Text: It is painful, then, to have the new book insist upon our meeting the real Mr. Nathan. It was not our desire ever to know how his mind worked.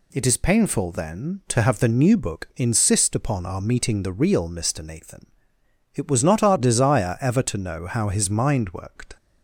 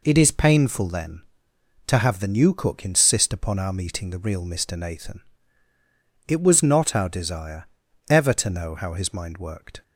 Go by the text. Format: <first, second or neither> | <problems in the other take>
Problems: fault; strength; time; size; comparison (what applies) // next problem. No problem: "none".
first | says "cook" for "book"; at 2.5 s // pauses between "desire" and "ever"; at 7.6 s; 0.44 s long